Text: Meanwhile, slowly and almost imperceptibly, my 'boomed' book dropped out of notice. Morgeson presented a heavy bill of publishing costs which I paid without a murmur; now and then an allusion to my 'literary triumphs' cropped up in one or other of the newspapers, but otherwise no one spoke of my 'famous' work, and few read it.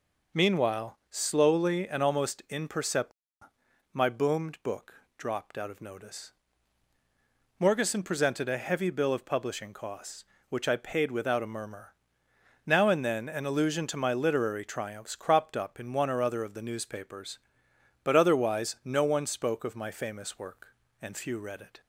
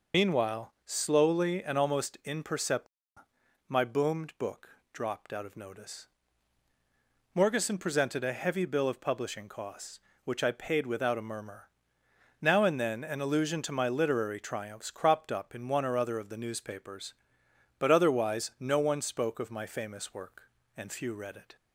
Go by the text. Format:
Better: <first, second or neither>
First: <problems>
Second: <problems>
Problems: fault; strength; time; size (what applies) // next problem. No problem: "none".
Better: first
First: pauses between "book" and "dropped"; slight; at 4.9 s; 0.22 s long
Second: loses the start of "Meanwhile"; at 0.1 s; 45 ms // pauses between "book" and "dropped"; slight; at 4.6 s; 0.22 s long